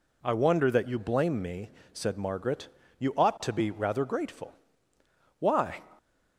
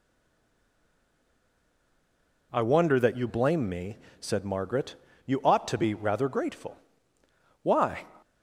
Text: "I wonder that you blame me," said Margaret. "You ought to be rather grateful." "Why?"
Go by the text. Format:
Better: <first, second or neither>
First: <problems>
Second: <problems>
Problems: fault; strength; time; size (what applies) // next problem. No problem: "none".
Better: first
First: none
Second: stays silent before the first word; until 2.5 s; 2.5 s long